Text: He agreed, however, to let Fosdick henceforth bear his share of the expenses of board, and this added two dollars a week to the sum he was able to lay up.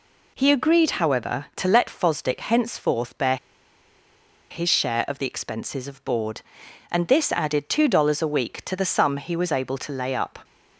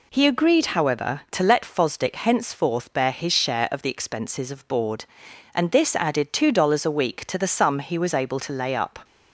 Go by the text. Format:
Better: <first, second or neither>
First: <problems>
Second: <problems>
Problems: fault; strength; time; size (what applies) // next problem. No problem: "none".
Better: second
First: pauses between "bear" and "his"; at 3.3 s; 1.1 s long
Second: none